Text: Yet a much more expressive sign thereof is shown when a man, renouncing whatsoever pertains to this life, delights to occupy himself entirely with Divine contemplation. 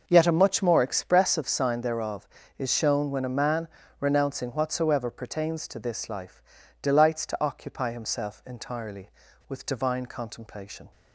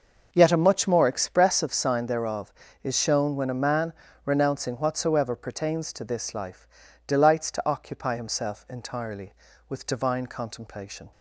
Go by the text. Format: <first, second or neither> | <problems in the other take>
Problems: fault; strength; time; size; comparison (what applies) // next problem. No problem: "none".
neither | none